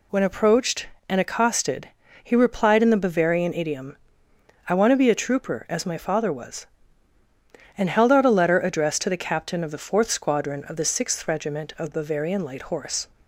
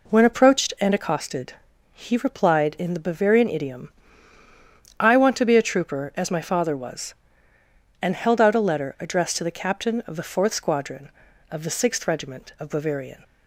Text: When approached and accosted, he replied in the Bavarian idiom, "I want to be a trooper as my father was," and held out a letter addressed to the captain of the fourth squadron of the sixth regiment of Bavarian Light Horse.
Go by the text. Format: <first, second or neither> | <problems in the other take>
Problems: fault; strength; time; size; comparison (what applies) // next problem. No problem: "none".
first | stops before "Light Horse"; at 13.2 s